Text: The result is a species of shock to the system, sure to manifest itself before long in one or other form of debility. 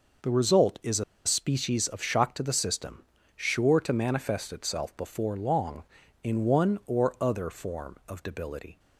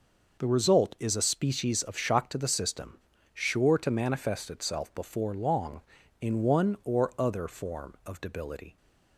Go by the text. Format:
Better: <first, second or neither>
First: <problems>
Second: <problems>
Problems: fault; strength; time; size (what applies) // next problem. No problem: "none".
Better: second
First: pauses between "a" and "species"; slight; at 1.0 s; 0.22 s long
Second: none